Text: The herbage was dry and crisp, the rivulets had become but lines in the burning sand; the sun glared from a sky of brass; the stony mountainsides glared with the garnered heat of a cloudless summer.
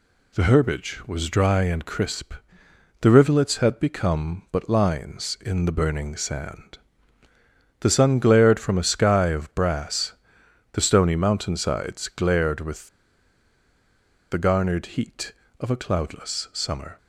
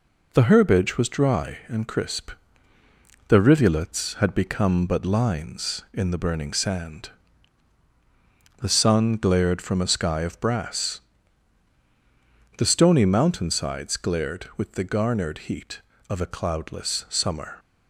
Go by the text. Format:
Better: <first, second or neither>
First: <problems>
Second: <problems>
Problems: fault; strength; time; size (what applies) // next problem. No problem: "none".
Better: second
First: pauses between "with" and "the"; strong; at 12.8 s; 1.4 s long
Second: none